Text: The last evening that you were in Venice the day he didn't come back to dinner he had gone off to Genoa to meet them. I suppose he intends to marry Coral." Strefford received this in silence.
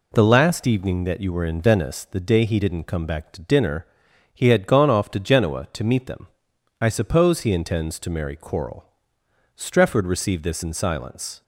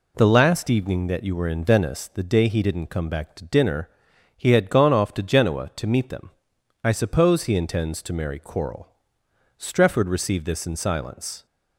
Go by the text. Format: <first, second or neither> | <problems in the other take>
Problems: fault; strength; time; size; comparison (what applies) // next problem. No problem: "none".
neither | pauses between "dinner" and "he"; noticeable; the same in both